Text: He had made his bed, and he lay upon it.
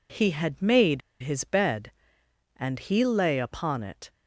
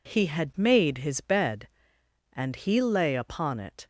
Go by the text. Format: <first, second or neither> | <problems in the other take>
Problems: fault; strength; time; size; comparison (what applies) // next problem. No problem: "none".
second | pauses between "made" and "his"; slight; at 1.0 s; 0.21 s long